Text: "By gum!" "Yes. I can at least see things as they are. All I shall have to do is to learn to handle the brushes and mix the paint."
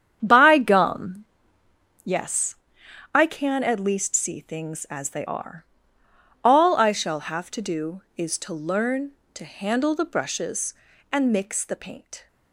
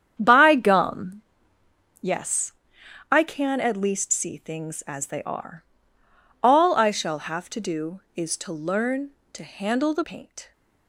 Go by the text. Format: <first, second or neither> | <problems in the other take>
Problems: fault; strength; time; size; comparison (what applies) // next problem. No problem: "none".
first | starts louder than the rest; strong; until 1.2 s; 8.5 dB; strong in the first // skips "brushes and mix the"; at 10.0 s